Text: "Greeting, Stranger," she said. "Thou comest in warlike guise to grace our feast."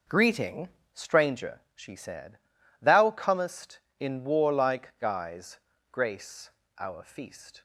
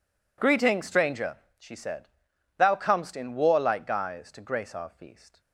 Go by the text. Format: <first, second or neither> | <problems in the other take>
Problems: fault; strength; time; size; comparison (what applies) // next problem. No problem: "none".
second | skips "to"; at 5.7 s // pauses between "grace" and "our"; slight; at 6.5 s; 0.28 s long